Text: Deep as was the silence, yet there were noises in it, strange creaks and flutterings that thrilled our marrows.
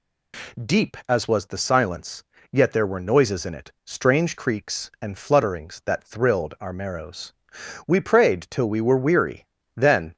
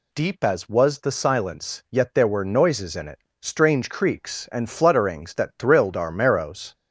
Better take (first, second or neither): second